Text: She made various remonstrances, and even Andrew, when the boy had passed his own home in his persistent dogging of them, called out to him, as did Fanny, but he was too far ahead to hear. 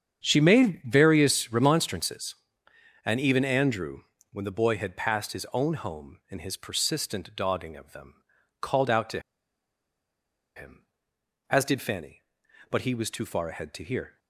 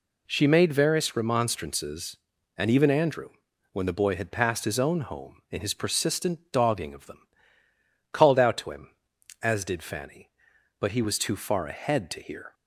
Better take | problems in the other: second | starts louder than the rest; strong; until 1.2 s; 7.5 dB // pauses between "to" and "him"; strong; at 9.2 s; 1.3 s long

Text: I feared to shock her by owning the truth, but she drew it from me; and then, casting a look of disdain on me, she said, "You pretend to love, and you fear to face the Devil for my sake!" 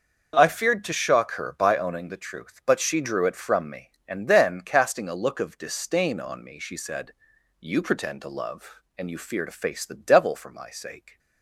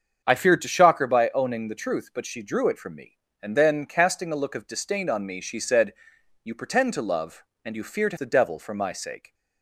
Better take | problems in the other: first | starts louder than the rest; until 1.2 s; 7 dB; noticeable in the first // skips "face"; at 8.1 s

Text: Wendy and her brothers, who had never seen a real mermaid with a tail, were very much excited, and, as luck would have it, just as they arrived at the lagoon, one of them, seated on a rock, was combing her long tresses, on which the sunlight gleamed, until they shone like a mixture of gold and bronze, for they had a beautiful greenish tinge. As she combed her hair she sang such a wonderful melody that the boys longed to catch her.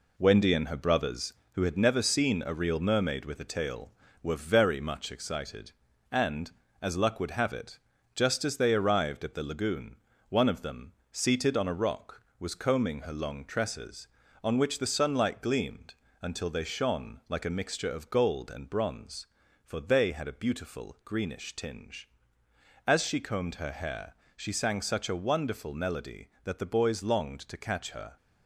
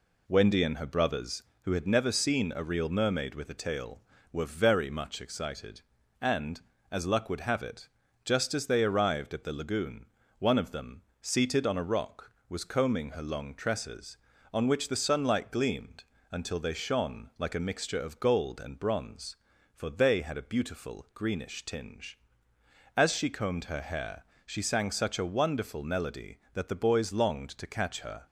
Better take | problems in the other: second | gets quieter; noticeable; throughout; 5.5 dB // pauses between "hair" and "she"; slight; at 24.1 s; 0.20 s long; slight in the second

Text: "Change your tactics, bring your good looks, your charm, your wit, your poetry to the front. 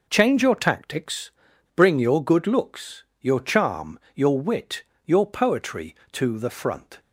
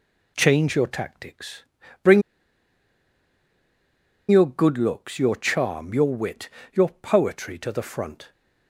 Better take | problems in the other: first | pauses between "bring" and "your"; strong; at 2.2 s; 2.0 s long

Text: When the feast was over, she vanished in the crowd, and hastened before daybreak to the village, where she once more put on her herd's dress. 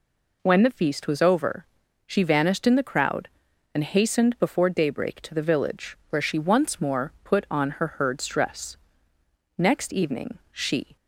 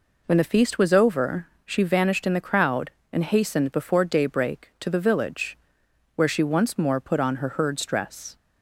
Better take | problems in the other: second | goes on to say "Next evening she"; from 9.5 s on; 1.3 s long

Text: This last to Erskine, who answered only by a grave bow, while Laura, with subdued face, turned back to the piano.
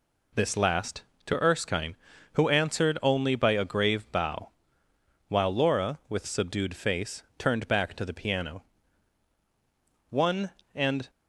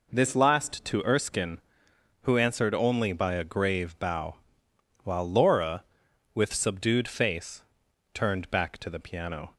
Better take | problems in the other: second | goes on to say "One and"; noticeable; from 10.0 s on; 1.0 s long

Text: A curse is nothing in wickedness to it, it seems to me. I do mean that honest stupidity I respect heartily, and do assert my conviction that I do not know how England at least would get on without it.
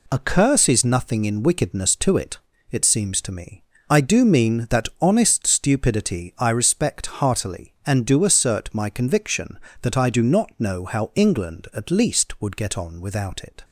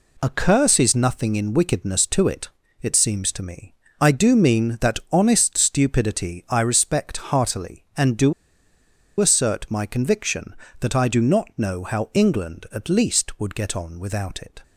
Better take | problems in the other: first | pauses between "do" and "assert"; noticeable; at 8.3 s; 0.87 s long

